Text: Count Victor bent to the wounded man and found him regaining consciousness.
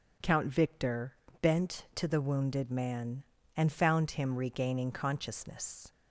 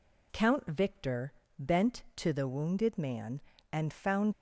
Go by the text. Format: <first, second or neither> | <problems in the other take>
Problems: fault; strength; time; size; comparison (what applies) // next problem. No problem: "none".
first | pauses between "Victor" and "bent"; slight; at 1.3 s; 0.26 s long; slight in the first // stops before "him regaining consciousness"; at 4.3 s